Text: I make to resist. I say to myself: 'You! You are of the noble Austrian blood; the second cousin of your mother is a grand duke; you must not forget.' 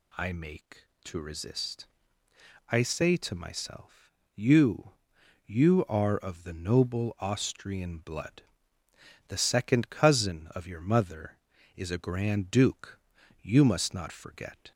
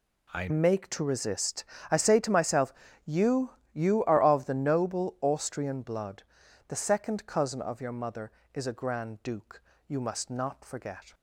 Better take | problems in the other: first | changes voice at "make"; from 0.4 s on; 10.7 s long

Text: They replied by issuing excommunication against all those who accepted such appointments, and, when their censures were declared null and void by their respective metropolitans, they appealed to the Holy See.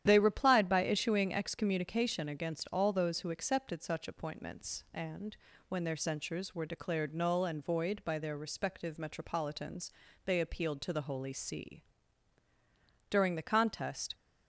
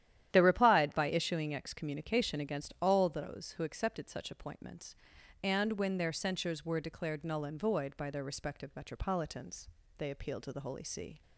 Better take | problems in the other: second | starts louder than the rest; strong; until 1.0 s; 10.5 dB; strong in the second // goes on to say "During the contest"; noticeable; from 13.1 s on; 1.0 s long

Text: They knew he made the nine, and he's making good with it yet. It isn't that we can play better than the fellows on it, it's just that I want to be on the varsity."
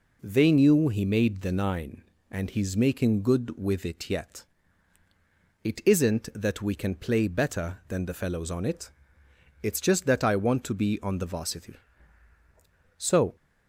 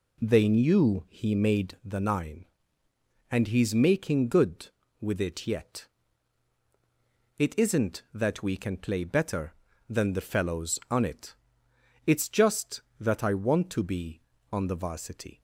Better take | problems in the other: second | goes on to say "So"; slight; from 12.9 s on; 0.38 s long

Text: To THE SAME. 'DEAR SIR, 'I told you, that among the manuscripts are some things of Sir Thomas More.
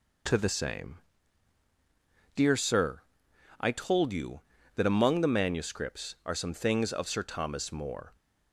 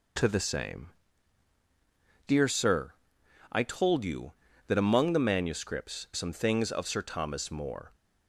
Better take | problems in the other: first | skips "are"; at 6.1 s

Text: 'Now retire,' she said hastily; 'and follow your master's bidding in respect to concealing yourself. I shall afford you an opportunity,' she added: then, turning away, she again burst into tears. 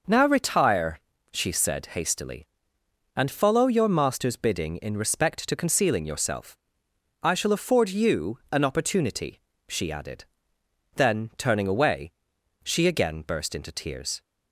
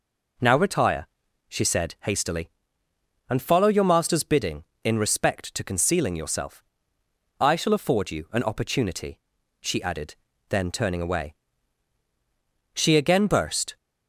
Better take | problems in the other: first | stops before "into tears"; at 13.7 s

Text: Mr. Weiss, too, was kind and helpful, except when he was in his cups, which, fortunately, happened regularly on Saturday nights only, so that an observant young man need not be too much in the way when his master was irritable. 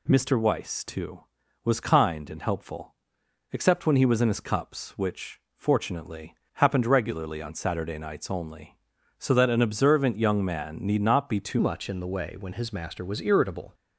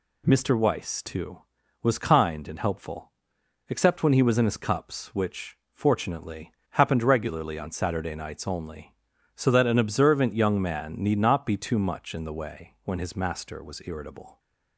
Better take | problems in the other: second | changes voice at "much"; from 11.5 s on; 2.2 s long

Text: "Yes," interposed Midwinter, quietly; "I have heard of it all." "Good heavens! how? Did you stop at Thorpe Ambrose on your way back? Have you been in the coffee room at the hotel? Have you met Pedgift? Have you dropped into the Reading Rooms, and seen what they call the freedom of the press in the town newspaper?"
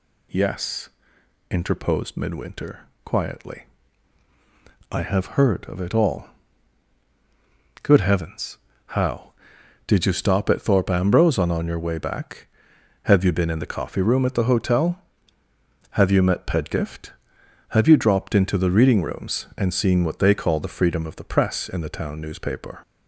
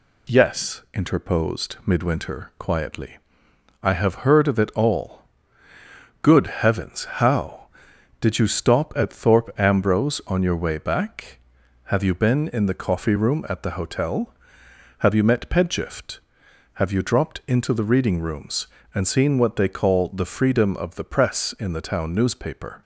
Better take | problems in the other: second | says "on" twice; at 11.5 s

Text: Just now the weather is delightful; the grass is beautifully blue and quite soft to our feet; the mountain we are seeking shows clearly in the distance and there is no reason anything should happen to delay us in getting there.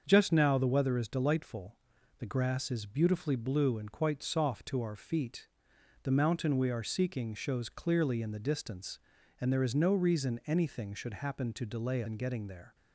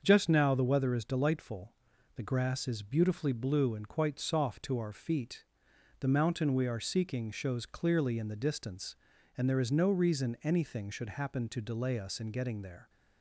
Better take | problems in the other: second | starts louder than the rest; until 1.0 s; 6.5 dB; also in the second // skips "us"; at 12.0 s

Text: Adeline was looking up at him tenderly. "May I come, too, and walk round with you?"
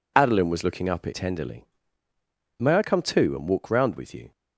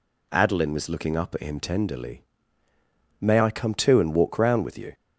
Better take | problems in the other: second | skips "him"; at 1.1 s

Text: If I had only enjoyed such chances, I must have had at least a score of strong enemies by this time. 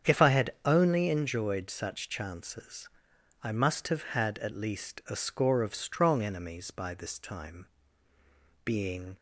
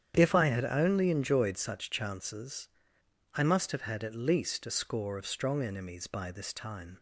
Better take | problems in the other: second | starts louder than the rest; strong; until 1.1 s; 8 dB; strong in the second // goes on to say "Being"; from 8.6 s on; 0.52 s long

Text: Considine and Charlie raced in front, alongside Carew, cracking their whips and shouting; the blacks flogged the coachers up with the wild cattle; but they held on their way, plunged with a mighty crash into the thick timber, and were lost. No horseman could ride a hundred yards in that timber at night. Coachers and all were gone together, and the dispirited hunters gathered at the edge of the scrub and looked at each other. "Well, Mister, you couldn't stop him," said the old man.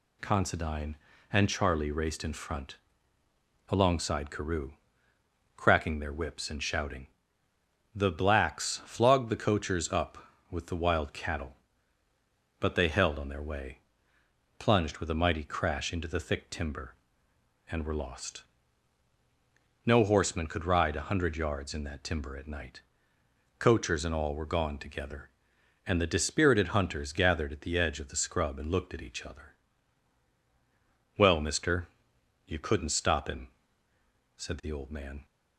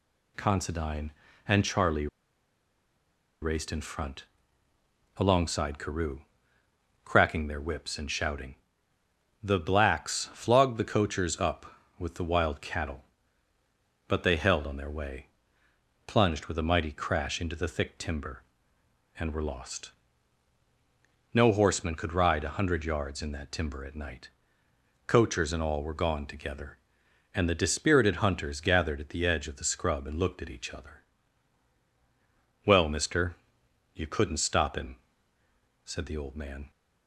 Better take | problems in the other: first | pauses between "Charlie" and "raced"; strong; at 2.0 s; 1.3 s long

